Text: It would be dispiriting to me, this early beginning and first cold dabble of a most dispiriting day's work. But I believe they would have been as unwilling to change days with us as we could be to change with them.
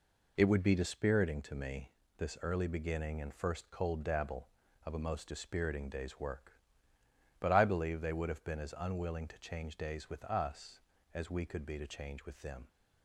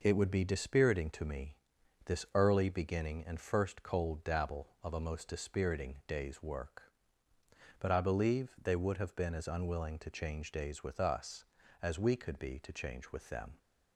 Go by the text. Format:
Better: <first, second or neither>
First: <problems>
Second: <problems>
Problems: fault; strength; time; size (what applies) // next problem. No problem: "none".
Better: neither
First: none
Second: none